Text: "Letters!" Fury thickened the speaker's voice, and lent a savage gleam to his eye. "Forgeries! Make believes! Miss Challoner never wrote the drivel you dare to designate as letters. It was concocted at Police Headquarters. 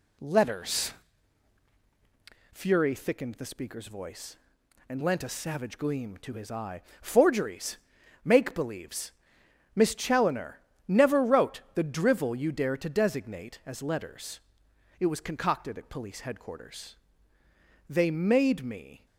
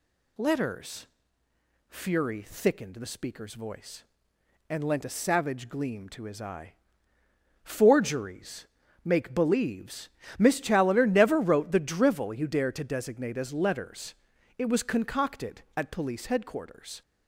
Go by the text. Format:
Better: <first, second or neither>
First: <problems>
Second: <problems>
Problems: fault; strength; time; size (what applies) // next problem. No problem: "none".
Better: second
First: pauses between "Challoner" and "never"; slight; at 10.6 s; 0.26 s long // goes on to say "They made me"; noticeable; from 17.8 s on; 1.1 s long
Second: none